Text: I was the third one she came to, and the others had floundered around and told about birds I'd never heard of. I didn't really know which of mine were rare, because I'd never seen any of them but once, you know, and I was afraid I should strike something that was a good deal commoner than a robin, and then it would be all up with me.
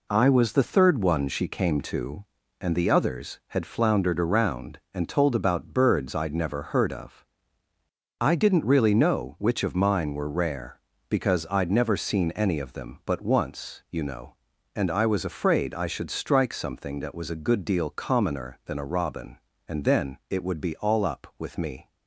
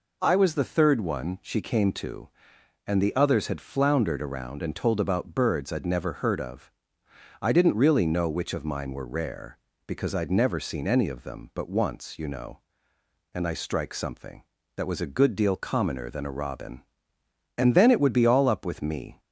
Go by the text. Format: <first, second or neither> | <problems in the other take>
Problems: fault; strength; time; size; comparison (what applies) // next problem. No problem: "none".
first | skips "was afraid I should"; at 13.5 s